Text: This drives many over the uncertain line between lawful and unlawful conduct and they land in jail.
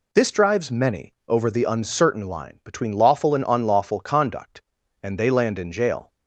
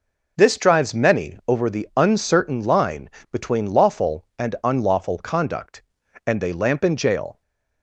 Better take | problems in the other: first | pauses between "line" and "between"; slight; at 3.0 s; 0.24 s long // says "lamp" for "land"; at 6.5 s // stays silent after the last word; slight; from 7.3 s on; 0.5 s long

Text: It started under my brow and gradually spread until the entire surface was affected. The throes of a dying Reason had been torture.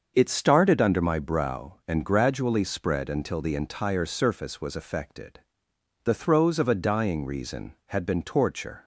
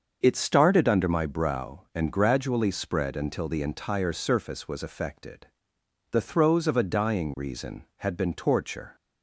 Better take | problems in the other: neither | starts louder than the rest; the same in both

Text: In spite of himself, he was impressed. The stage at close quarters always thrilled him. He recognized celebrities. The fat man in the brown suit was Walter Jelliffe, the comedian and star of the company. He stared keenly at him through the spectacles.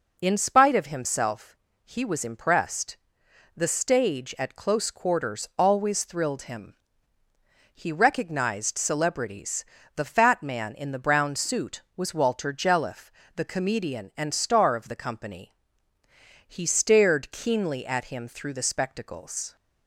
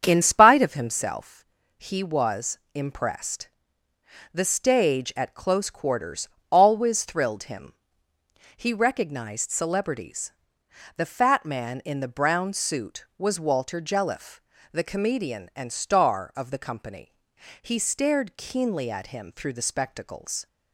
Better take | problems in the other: first | starts louder than the rest; strong; until 1.1 s; 7.5 dB // pauses between "was" and "impressed"; slight; at 2.5 s; 0.16 s long // pauses between "quarters" and "always"; slight; at 6.2 s; 0.24 s long

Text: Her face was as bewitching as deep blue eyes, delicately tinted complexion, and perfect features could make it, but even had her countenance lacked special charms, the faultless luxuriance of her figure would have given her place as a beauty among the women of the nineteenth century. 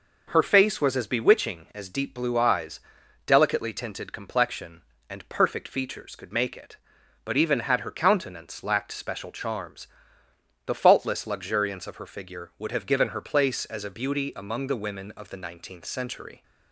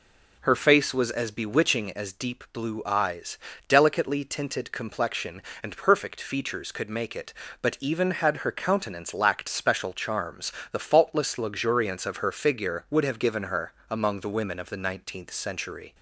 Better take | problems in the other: first | skips "place as a beauty"; at 13.8 s

